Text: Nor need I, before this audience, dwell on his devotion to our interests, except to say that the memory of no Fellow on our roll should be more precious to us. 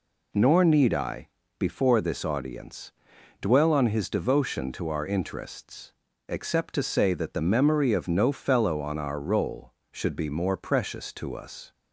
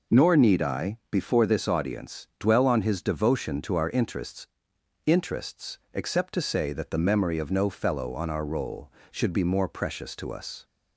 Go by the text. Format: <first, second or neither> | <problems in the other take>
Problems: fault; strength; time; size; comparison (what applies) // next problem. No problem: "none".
first | says "interests" twice; at 5.0 s